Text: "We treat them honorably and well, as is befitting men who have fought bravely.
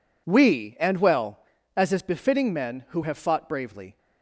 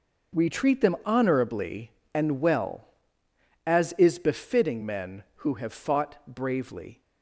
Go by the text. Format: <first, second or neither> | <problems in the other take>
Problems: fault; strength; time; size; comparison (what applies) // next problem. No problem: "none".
second | skips "treat them honorably"; at 0.7 s